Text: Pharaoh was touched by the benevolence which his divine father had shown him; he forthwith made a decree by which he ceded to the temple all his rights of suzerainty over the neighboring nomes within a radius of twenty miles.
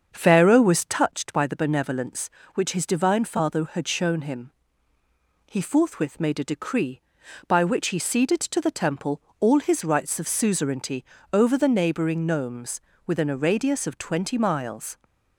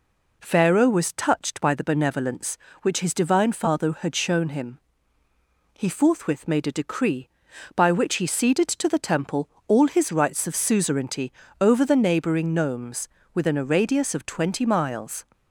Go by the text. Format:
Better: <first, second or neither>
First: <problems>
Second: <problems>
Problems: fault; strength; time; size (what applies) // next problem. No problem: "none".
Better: second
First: starts louder than the rest; until 1.0 s; 7 dB // pauses between "temple" and "all"; slight; at 9.2 s; 0.18 s long // pauses between "suzerainty" and "over"; slight; at 11.0 s; 0.30 s long // pauses between "nomes" and "within"; slight; at 12.7 s; 0.28 s long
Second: pauses between "temple" and "all"; slight; at 9.4 s; 0.18 s long // pauses between "suzerainty" and "over"; slight; at 11.3 s; 0.30 s long // pauses between "nomes" and "within"; slight; at 13.0 s; 0.28 s long